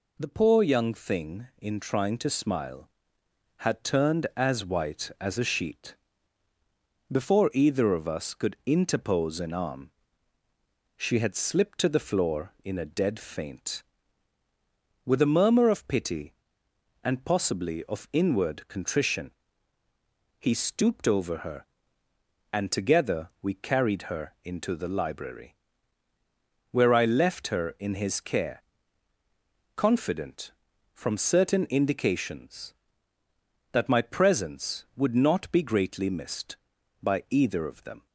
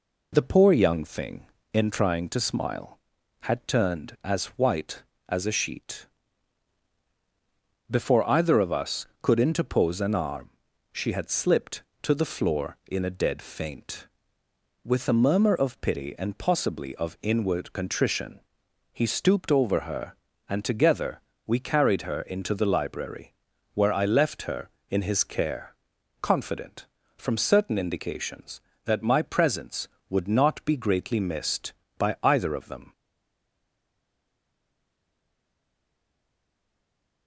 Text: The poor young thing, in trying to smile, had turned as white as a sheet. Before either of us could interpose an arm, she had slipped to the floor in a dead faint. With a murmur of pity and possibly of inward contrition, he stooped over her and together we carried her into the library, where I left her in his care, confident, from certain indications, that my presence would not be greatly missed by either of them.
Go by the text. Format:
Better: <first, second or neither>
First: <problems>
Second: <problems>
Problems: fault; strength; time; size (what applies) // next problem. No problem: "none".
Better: first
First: none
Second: pauses between "together" and "we"; slight; at 21.1 s; 0.26 s long // stays silent after the last word; strong; from 32.9 s on; 4.3 s long